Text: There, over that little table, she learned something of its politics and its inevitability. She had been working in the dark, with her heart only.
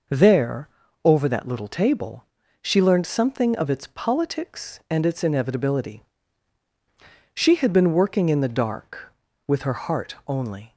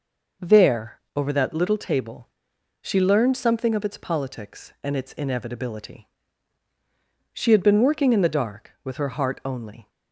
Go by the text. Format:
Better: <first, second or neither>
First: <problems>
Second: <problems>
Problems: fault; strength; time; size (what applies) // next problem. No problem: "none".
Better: neither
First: none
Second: none